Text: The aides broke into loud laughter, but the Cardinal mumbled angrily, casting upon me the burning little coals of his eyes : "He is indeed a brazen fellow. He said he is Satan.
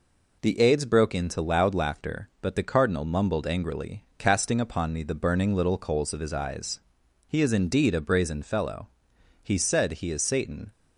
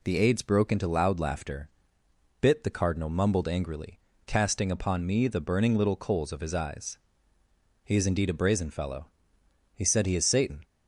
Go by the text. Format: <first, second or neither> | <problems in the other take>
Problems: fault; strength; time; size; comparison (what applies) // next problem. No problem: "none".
first | says "bit" for "but"; at 2.4 s